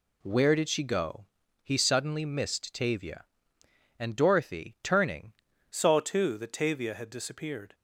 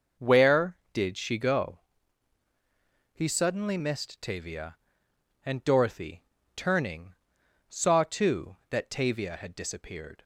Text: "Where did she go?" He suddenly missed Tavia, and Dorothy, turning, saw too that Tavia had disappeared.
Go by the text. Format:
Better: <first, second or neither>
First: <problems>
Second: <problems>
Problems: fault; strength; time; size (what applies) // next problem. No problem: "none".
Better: second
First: changes voice at "saw"; from 5.7 s on; 2.0 s long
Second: none